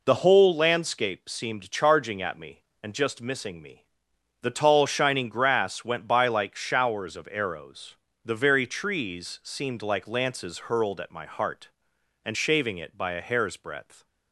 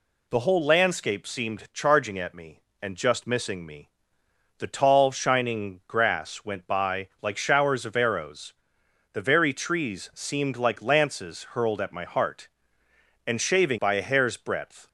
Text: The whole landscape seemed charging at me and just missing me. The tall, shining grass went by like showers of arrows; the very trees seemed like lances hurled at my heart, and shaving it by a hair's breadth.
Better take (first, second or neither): first